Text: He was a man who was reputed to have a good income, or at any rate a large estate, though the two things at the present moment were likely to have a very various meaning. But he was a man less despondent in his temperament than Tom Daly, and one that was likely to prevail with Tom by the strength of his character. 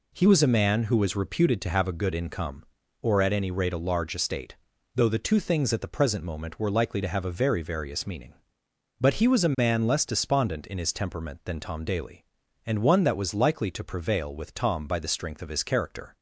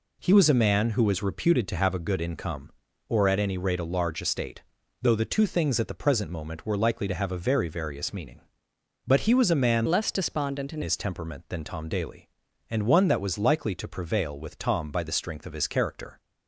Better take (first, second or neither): first